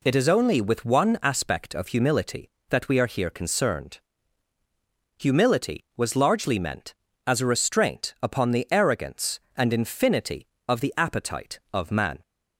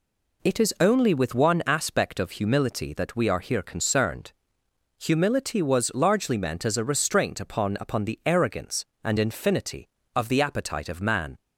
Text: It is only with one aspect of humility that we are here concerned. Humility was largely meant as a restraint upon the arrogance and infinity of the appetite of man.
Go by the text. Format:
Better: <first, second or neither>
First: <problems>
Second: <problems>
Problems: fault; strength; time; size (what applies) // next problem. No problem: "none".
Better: first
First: none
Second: says "upon" twice; at 7.8 s